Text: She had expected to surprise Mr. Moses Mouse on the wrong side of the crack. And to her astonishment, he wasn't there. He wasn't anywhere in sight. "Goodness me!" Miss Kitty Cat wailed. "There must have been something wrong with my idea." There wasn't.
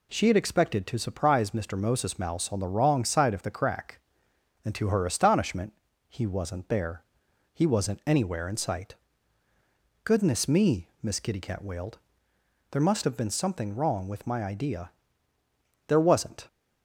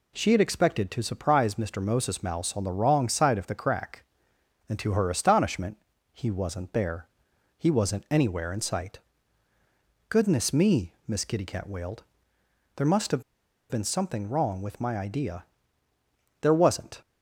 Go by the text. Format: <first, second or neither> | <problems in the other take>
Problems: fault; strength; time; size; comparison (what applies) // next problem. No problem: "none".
first | pauses between "have" and "been"; noticeable; at 13.2 s; 0.48 s long